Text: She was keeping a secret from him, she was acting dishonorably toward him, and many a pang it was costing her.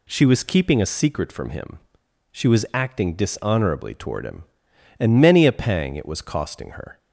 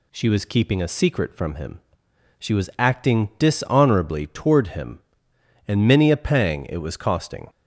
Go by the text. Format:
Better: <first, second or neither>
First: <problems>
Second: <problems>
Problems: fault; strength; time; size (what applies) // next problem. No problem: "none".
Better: first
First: none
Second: stops before "her"; at 7.4 s